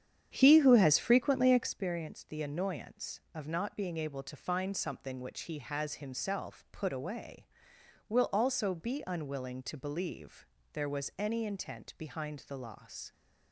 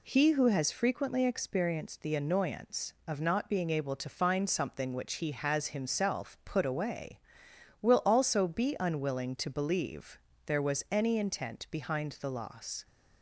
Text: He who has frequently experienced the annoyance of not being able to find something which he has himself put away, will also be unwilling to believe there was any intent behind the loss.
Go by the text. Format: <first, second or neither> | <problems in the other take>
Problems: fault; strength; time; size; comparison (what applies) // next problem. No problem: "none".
second | starts louder than the rest; strong; until 1.8 s; 9 dB // pauses between "believe" and "there"; slight; at 10.4 s; 0.26 s long; slight in the second